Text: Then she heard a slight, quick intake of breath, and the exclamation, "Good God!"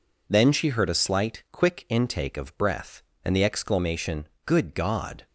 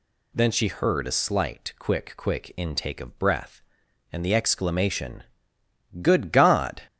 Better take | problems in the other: first | says "quick" twice; at 2.1 s

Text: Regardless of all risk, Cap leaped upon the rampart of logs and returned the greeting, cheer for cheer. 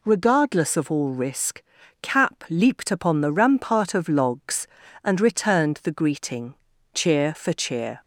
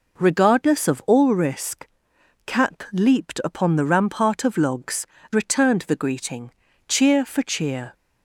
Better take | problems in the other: first | skips "and"; at 5.1 s

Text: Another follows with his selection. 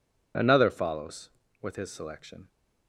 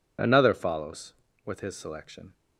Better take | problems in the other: neither | none

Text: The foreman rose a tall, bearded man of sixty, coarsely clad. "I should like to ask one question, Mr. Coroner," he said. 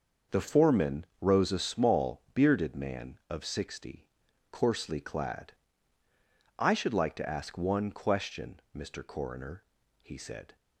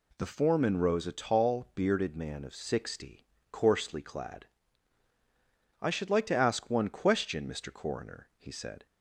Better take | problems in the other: second | starts louder than the rest; until 1.4 s; 6 dB // says "small" for "tall"; at 1.5 s

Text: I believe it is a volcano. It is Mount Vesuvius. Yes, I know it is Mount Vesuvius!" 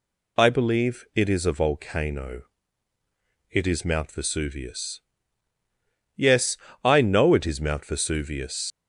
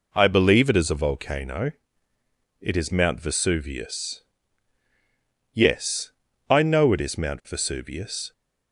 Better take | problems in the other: second | leaves "Vesuvius" unfinished; at 8.7 s; 80 ms

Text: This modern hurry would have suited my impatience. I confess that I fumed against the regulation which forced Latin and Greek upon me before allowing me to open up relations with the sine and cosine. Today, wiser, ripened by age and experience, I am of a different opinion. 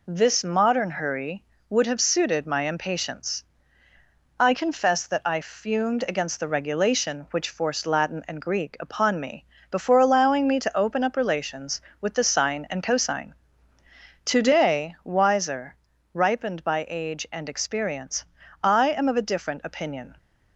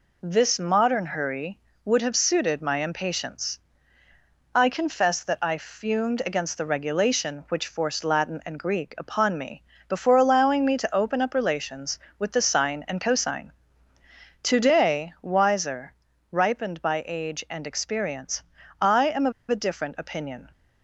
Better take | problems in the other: first | pauses between "me" and "before"; slight; at 9.6 s; 0.28 s long; slight in the first // pauses between "of" and "a"; slight; at 19.3 s; 0.17 s long

